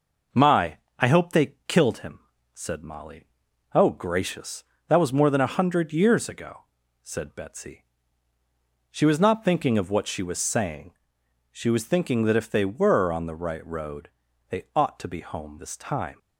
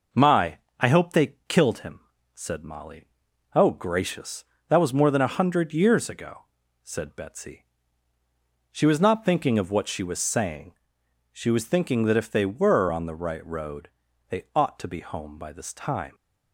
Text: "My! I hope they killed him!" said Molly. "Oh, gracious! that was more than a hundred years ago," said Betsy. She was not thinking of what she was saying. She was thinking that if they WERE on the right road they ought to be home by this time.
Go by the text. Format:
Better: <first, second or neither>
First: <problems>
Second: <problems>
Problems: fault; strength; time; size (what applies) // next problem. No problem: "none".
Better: second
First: pauses between "road" and "they"; at 14.0 s; 0.42 s long // skips "by"; at 15.5 s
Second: pauses between "road" and "they"; at 13.8 s; 0.42 s long